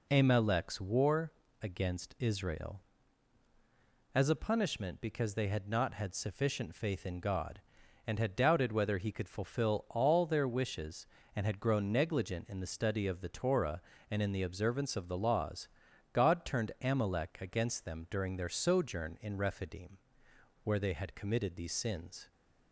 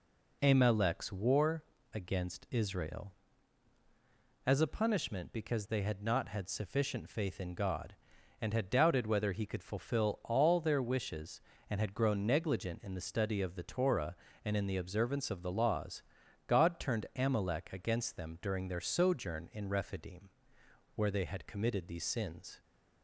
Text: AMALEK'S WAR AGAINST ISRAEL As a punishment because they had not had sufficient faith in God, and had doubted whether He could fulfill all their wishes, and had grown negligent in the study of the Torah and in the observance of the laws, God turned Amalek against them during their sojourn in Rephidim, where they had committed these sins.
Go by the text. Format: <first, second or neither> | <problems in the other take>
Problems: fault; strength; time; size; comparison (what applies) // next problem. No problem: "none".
neither | pauses between "WAR" and "AGAINST"; slight; the same in both